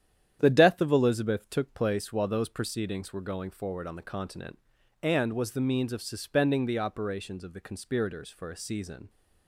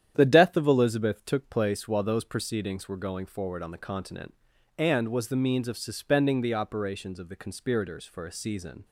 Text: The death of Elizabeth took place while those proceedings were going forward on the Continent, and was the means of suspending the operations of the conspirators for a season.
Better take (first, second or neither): neither